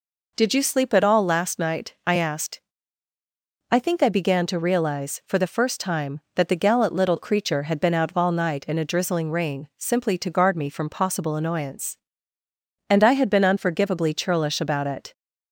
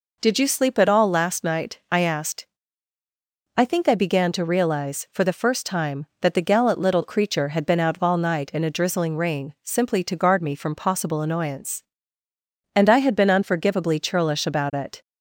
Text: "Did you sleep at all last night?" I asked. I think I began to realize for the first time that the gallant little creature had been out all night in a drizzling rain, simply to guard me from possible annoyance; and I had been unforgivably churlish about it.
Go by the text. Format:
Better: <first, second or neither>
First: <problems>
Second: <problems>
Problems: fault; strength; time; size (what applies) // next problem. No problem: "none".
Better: neither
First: none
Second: none